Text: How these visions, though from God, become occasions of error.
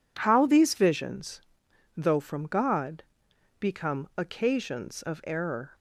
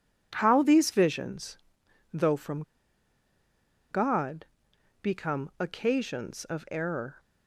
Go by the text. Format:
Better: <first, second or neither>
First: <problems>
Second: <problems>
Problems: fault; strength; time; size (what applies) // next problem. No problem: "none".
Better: first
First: none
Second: pauses between "from" and "God"; strong; at 2.6 s; 1.2 s long